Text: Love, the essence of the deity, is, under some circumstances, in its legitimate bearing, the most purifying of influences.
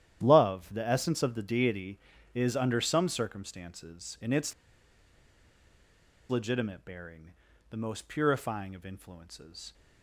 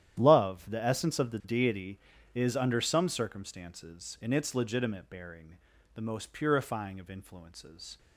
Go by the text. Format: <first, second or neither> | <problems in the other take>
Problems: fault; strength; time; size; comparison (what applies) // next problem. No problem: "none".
second | starts louder than the rest; strong; until 1.2 s; 11 dB; strong in the second // pauses between "its" and "legitimate"; strong; at 4.5 s; 1.7 s long